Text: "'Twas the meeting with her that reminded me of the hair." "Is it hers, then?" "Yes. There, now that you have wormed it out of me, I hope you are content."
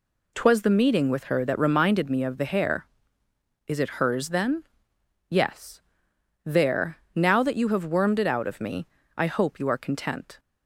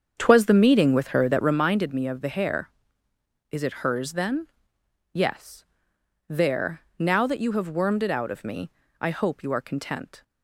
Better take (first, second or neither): first